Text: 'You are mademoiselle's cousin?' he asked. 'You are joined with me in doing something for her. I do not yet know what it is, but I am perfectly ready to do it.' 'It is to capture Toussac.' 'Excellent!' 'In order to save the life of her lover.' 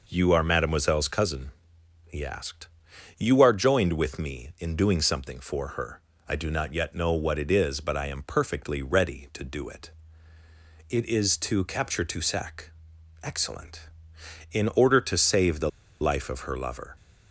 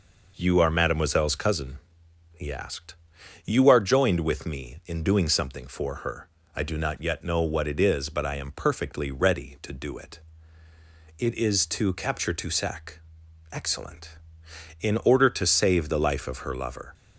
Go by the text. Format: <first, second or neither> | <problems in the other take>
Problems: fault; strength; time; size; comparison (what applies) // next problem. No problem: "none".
second | pauses between "the" and "life"; slight; at 15.6 s; 0.31 s long